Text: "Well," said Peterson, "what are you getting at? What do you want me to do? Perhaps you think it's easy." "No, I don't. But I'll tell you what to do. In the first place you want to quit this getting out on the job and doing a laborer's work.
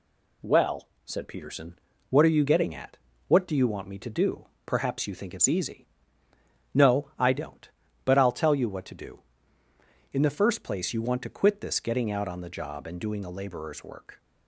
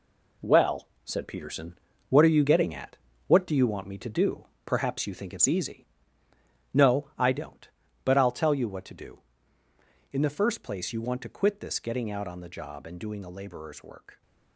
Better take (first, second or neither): first